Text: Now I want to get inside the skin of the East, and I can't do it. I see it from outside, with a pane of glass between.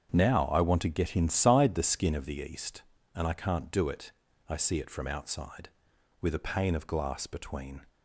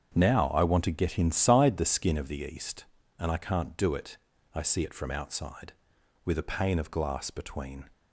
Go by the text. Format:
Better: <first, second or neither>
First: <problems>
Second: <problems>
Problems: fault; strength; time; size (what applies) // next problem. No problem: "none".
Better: neither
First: starts louder than the rest; strong; until 1.1 s; 7.5 dB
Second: starts louder than the rest; strong; until 1.1 s; 7.5 dB